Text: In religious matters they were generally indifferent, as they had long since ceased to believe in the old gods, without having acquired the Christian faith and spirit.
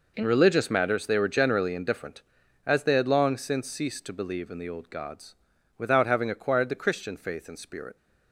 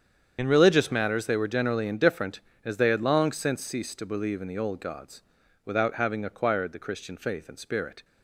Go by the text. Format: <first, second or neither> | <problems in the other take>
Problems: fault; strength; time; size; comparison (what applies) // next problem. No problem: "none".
first | loses the start of "In"; at 0.3 s; 65 ms // starts louder than the rest; strong; until 1.3 s; 8 dB